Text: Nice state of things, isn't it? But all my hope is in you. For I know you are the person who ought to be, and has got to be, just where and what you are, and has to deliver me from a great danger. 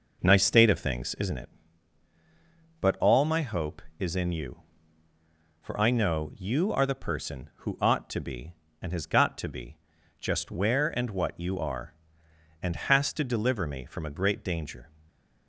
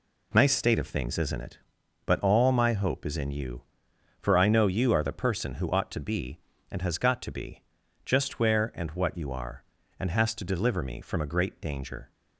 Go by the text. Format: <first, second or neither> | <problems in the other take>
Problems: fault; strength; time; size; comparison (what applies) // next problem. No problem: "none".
second | starts louder than the rest; noticeable; until 1.4 s; 5 dB // stays silent after the last word; slight; from 14.8 s on; 0.6 s long